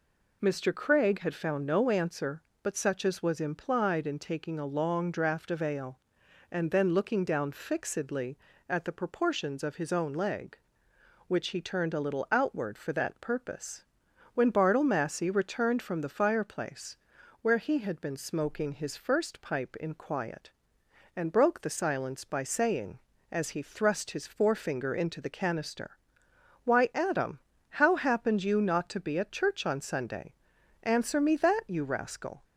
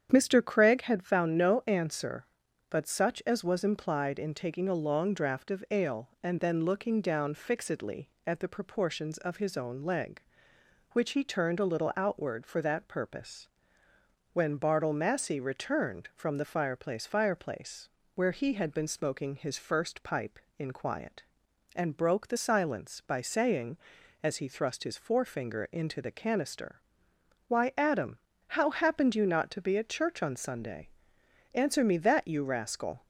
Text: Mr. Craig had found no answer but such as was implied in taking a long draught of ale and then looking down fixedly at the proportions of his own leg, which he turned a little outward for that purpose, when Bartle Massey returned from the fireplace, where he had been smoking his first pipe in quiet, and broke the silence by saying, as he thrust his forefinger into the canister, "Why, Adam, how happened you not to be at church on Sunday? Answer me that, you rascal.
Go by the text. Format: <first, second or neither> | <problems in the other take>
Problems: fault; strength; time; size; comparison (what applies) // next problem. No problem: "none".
first | starts louder than the rest; strong; until 1.1 s; 8.5 dB // says "fireplace" twice; at 17.0 s